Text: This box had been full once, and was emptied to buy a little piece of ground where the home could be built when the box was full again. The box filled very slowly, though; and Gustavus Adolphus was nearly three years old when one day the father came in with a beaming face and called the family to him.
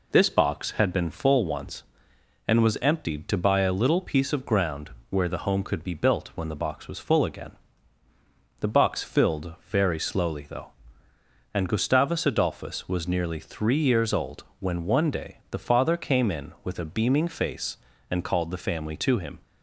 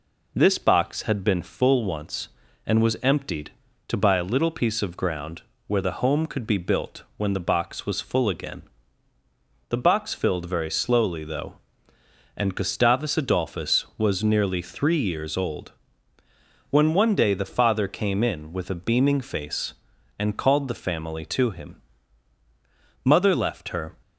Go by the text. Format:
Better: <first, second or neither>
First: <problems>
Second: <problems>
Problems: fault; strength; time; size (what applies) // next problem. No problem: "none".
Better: first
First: pauses between "ground" and "where"; slight; at 4.9 s; 0.20 s long // pauses between "old" and "when"; slight; at 14.4 s; 0.16 s long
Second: pauses between "ground" and "where"; slight; at 5.4 s; 0.26 s long // pauses between "old" and "when"; noticeable; at 15.7 s; 0.98 s long // goes on to say "Mother left her"; noticeable; from 23.0 s on; 0.90 s long